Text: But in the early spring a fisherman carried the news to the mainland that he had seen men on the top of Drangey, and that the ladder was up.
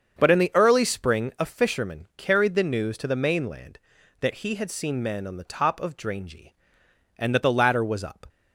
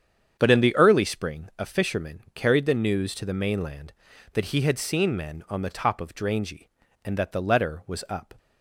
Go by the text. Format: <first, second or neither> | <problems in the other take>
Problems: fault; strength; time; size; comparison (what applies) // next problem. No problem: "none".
first | starts louder than the rest; strong; until 1.4 s; 8 dB; also in the first // says "letter" for "ladder"; at 7.4 s